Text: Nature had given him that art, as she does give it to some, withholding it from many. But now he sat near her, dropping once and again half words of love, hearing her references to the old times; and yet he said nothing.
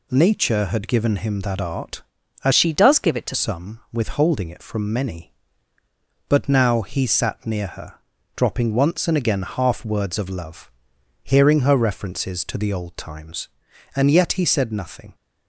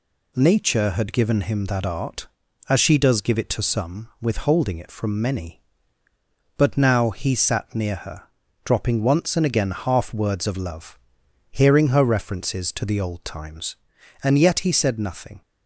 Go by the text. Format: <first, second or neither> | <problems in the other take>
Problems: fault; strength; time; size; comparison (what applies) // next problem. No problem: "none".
second | changes voice from "she" to "to"; from 2.5 to 3.3 s; 0.8 s long